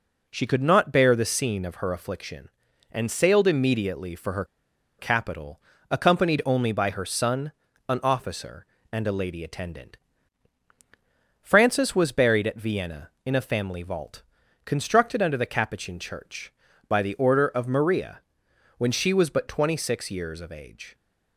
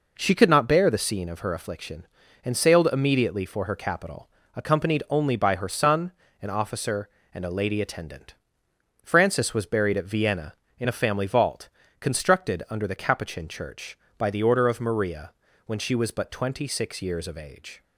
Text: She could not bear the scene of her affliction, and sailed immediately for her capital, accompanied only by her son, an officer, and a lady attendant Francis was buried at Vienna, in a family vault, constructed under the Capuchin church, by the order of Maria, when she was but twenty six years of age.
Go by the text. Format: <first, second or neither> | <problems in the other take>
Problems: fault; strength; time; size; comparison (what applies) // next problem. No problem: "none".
second | pauses between "her" and "capital"; noticeable; at 4.4 s; 0.54 s long // pauses between "attendant" and "Francis"; strong; at 9.9 s; 1.4 s long; noticeable in the second